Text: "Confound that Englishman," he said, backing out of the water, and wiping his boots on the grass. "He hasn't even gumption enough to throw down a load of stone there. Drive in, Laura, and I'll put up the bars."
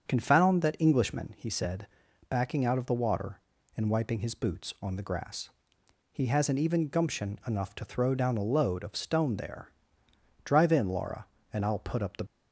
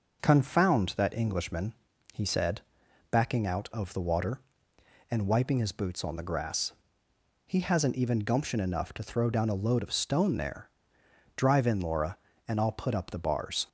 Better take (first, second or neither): second